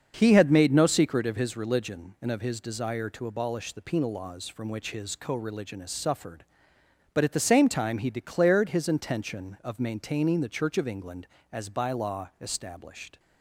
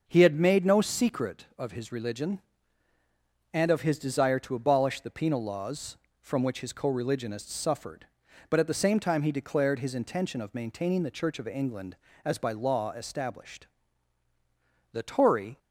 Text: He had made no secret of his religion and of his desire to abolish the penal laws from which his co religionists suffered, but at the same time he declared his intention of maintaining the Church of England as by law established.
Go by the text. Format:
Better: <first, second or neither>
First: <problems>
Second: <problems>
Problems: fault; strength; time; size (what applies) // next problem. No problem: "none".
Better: first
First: starts louder than the rest; until 1.1 s; 6.5 dB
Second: starts louder than the rest; until 1.0 s; 6 dB // goes on to say "The Tory"; noticeable; from 14.9 s on; 0.66 s long